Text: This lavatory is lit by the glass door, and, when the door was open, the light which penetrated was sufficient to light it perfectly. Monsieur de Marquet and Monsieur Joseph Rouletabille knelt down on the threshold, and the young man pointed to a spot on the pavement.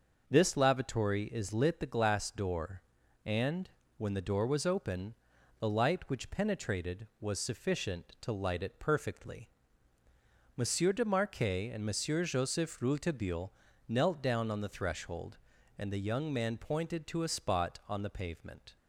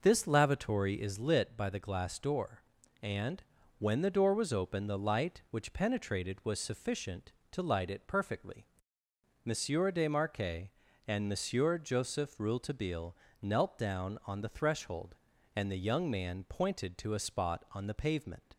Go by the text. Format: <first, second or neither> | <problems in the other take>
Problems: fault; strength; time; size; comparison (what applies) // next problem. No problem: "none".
second | starts louder than the rest; until 1.2 s; 6 dB // skips "by"; at 1.7 s // pauses between "Rouletabille" and "knelt"; slight; at 13.5 s; 0.36 s long; slight in the second